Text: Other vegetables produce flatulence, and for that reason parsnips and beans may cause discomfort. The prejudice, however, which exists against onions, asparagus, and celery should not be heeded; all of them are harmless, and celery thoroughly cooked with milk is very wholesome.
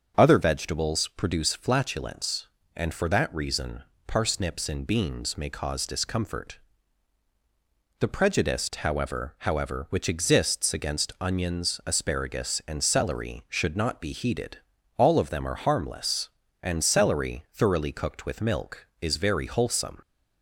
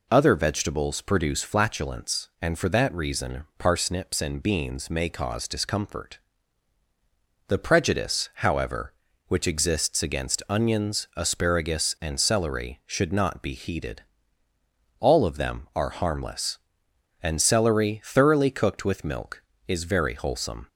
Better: second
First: starts louder than the rest; until 1.1 s; 6.5 dB // pauses between "reason" and "parsnips"; slight; at 3.8 s; 0.24 s long // says "however" twice; at 9.3 s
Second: none

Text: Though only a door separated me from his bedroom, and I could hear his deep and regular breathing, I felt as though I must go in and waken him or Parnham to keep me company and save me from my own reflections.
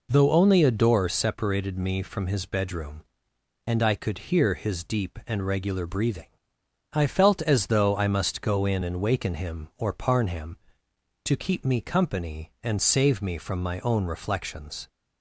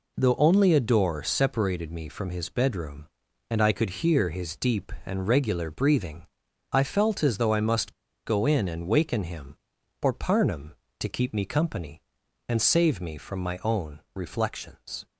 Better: first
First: none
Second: pauses between "must" and "go"; slight; at 7.9 s; 0.33 s long

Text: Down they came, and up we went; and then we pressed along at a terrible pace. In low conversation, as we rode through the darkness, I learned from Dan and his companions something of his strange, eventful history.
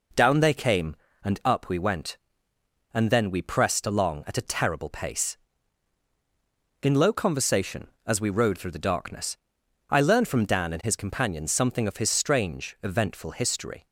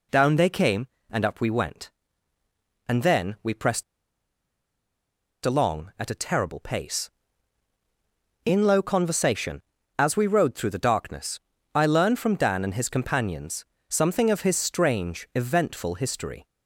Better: first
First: none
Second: pauses between "pressed" and "along"; strong; at 3.8 s; 1.6 s long // pauses between "companions" and "something"; slight; at 13.6 s; 0.24 s long

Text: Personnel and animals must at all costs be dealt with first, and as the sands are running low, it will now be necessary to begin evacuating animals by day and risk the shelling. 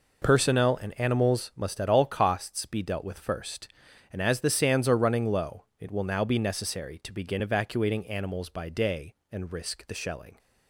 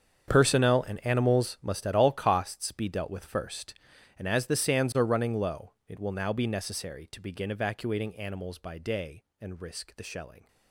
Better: first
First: none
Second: gets quieter; strong; throughout; 16 dB

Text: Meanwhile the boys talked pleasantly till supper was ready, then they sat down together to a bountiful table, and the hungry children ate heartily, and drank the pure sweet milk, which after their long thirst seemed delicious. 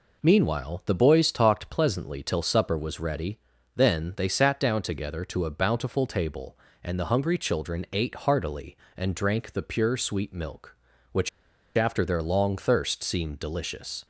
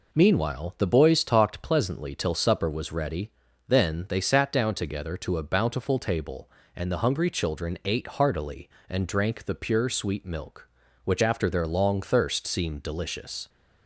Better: second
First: pauses between "which" and "after"; noticeable; at 11.2 s; 0.48 s long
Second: none

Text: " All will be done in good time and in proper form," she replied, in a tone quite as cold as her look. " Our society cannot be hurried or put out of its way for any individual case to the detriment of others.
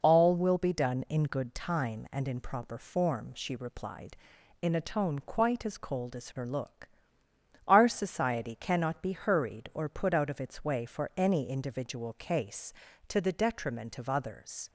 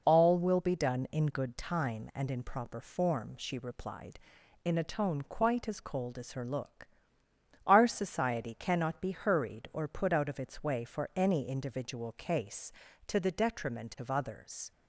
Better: neither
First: none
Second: none

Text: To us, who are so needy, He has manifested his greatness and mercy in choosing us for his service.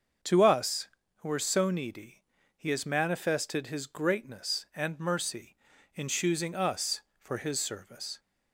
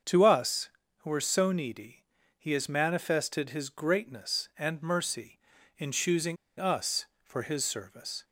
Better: first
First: starts louder than the rest; until 1.5 s; 6.5 dB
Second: starts louder than the rest; until 1.3 s; 6.5 dB // pauses between "choosing" and "us"; slight; at 6.3 s; 0.23 s long

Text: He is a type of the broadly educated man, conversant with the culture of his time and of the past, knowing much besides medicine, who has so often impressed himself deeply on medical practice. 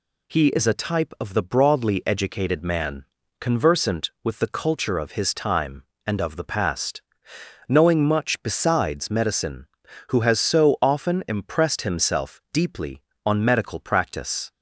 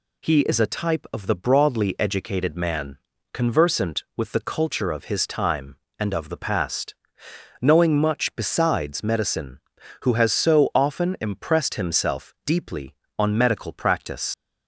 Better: first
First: none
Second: leaves "practice" unfinished; at 14.3 s; 100 ms

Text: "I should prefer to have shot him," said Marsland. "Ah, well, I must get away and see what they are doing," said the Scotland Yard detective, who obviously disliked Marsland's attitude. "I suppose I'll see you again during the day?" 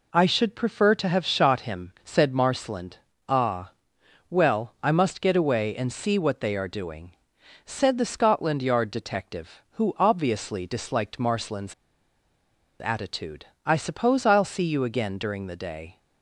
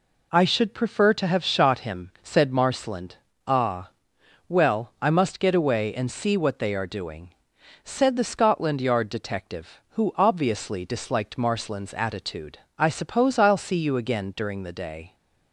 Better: second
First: pauses between "Marsland's" and "attitude"; at 11.7 s; 1.0 s long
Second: none

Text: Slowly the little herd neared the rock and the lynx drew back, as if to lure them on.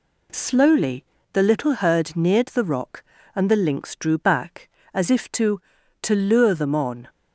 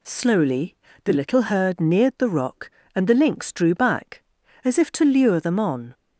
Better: second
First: pauses between "Slowly" and "the"; slight; at 1.0 s; 0.30 s long // says "to" twice; at 6.0 s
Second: pauses between "Slowly" and "the"; slight; at 0.7 s; 0.28 s long

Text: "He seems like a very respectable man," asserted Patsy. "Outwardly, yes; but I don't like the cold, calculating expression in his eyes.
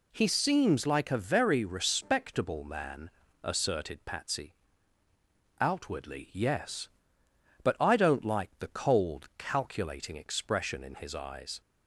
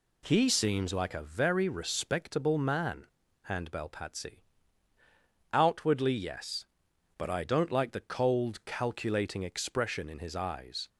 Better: first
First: none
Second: says "handbell" for "asserted"; at 3.4 s

